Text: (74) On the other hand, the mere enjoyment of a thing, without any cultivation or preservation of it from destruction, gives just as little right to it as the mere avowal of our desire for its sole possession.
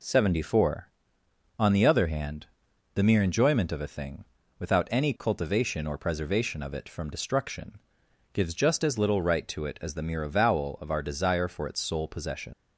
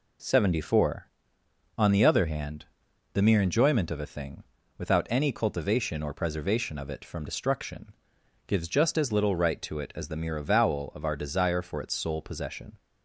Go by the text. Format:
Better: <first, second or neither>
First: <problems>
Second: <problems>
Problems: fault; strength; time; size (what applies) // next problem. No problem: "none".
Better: second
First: leaves "possession" unfinished; at 12.5 s; 115 ms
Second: none